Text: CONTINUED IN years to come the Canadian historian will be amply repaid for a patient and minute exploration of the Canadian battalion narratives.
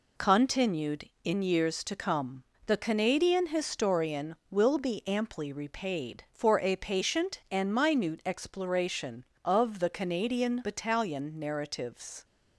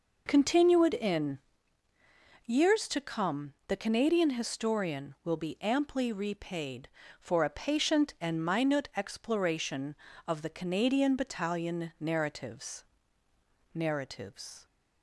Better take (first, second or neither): first